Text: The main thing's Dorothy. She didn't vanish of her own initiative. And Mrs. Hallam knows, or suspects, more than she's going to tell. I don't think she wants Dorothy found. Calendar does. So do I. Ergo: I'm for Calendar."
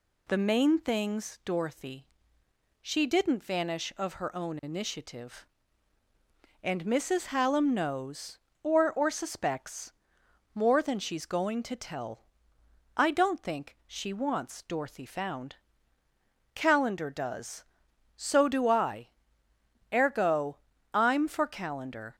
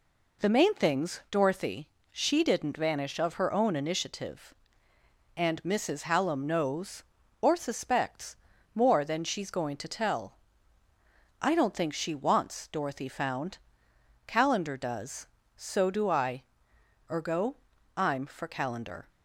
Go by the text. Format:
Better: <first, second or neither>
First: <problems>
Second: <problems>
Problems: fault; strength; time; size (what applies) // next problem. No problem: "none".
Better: second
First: says "or" twice; at 8.9 s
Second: none